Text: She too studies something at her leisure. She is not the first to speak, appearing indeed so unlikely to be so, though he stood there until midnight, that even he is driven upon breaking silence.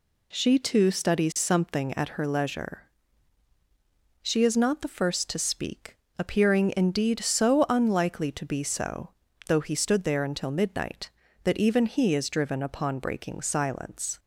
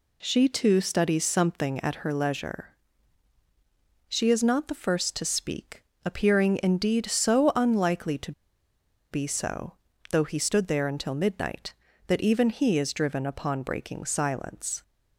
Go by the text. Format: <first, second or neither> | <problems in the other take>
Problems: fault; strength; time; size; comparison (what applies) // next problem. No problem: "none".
first | pauses between "to" and "be"; noticeable; at 8.3 s; 0.80 s long